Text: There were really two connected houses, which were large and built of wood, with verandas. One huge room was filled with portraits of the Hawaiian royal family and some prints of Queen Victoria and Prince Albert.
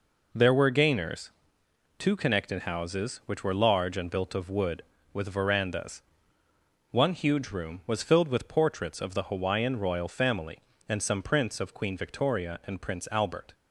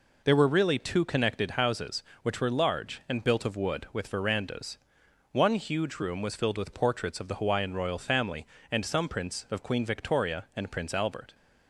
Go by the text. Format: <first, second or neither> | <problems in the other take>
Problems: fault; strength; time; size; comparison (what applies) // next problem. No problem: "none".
second | says "gainers" for "really"; at 0.6 s